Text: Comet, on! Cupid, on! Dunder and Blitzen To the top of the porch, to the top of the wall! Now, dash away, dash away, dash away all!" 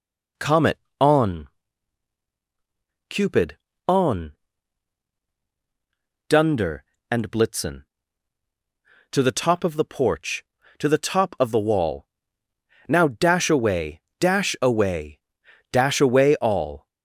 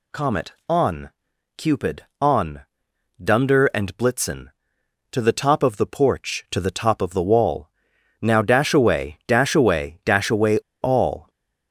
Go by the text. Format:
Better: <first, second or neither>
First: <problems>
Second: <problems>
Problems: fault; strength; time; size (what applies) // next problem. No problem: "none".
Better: first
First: none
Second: pauses between "away" and "all"; slight; at 10.5 s; 0.25 s long